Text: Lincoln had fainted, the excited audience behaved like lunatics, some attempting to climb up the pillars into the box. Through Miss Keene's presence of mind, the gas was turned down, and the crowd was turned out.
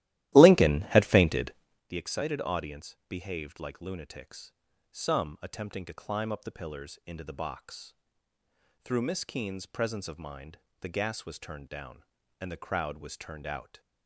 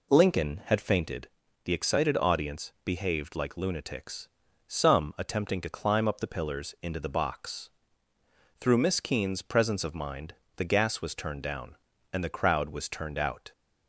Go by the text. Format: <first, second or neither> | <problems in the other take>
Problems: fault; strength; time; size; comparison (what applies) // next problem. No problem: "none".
second | starts louder than the rest; strong; until 1.9 s; 15 dB